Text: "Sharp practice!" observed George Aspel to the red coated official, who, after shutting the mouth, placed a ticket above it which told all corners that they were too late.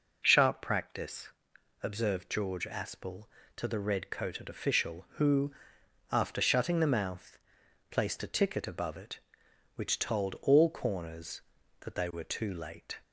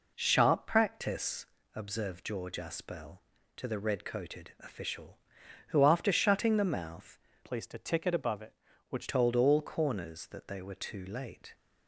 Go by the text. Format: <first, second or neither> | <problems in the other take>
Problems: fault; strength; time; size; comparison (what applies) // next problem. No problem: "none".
first | changes voice from "placed" to "which"; from 7.4 to 9.0 s; 1.6 s long